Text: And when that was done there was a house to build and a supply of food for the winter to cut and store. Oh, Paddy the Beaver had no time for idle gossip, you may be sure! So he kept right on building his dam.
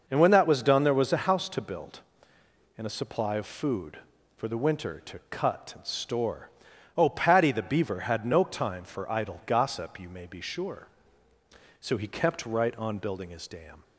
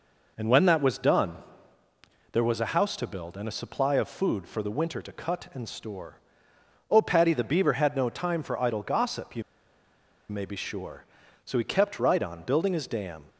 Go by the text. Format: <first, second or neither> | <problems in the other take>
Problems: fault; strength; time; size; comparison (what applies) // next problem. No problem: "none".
first | pauses between "done" and "there"; noticeable; at 1.3 s; 0.96 s long // pauses between "you" and "may"; noticeable; at 9.4 s; 0.86 s long